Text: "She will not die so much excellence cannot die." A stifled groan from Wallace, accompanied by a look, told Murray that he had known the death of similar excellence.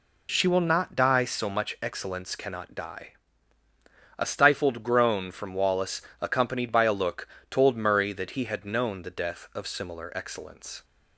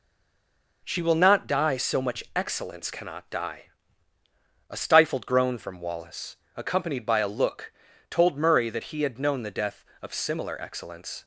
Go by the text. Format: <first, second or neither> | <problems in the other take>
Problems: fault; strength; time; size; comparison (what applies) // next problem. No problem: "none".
first | stays silent before the first word; slight; until 0.8 s; 0.8 s long